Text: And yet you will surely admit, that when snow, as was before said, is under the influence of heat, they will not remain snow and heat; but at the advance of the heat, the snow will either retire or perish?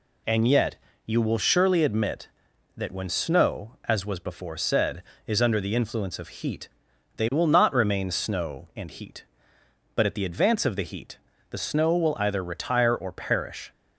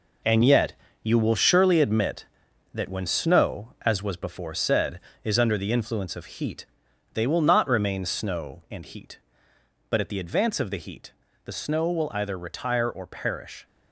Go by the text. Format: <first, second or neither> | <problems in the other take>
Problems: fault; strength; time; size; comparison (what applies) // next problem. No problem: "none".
first | gets quieter; strong; throughout; 8 dB // pauses between "yet" and "you"; slight; at 0.7 s; 0.30 s long; slight in the first